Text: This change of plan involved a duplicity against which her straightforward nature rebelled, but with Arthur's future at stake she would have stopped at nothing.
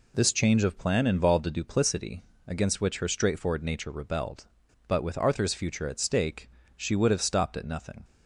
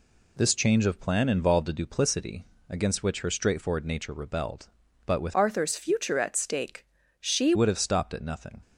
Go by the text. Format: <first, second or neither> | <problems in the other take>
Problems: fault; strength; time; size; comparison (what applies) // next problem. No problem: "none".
first | pauses between "duplicity" and "against"; slight; at 2.4 s; 0.24 s long; slight in the first // changes voice from "Arthur's" to "she"; from 5.3 to 7.5 s; 2.2 s long // pauses between "stake" and "she"; slight; at 6.8 s; 0.32 s long; slight in the first